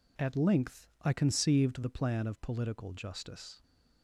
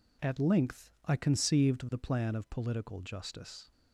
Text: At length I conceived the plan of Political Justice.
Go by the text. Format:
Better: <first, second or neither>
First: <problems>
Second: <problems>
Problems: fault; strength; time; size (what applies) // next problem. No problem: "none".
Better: neither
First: none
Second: none